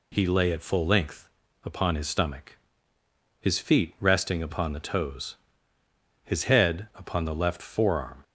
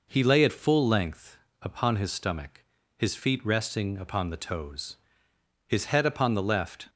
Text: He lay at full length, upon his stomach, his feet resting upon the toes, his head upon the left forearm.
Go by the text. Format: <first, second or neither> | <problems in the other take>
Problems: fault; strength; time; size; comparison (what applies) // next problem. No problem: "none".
first | stops before "forearm"; at 6.8 s